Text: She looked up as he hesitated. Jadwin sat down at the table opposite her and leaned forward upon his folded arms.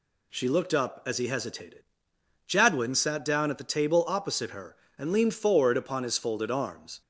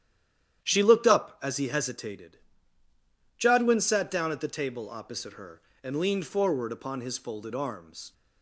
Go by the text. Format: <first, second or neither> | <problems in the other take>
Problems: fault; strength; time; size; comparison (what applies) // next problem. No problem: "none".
first | stays silent before the first word; slight; until 0.6 s; 0.6 s long // starts louder than the rest; strong; until 1.6 s; 10.5 dB